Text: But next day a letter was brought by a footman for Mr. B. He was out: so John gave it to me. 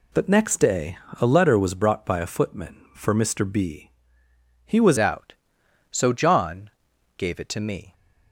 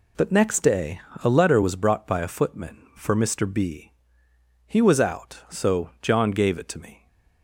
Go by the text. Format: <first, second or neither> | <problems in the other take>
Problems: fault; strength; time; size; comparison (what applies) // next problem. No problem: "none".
second | pauses between "day" and "a"; slight; at 0.9 s; 0.22 s long; slight in the second // changes voice at "out"; from 4.9 s on; 3.0 s long // pauses between "John" and "gave"; noticeable; at 6.7 s; 0.46 s long